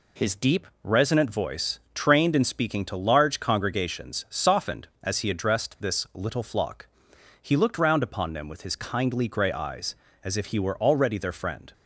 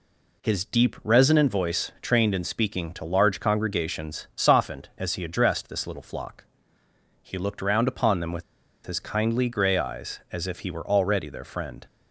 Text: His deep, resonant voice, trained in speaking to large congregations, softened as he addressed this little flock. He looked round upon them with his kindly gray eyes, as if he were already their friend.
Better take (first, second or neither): first